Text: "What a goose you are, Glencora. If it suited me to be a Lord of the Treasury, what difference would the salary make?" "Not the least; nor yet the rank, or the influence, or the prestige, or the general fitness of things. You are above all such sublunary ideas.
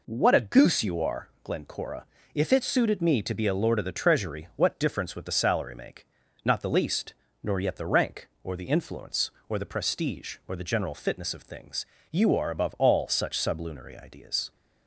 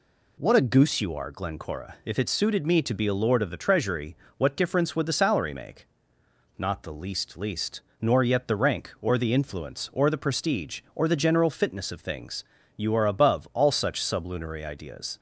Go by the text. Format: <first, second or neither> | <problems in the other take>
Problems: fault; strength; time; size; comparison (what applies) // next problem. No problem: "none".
first | says "least" twice; at 7.3 s